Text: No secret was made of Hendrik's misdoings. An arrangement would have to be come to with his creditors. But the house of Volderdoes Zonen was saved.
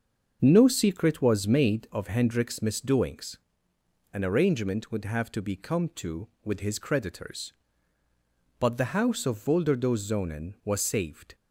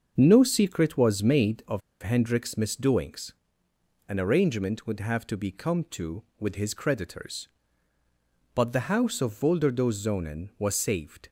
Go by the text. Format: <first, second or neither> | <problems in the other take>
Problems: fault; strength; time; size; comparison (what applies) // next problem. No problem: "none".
first | starts louder than the rest; until 1.1 s; 6.5 dB; also in the first // pauses between "of" and "Hendrik's"; slight; at 1.8 s; 0.22 s long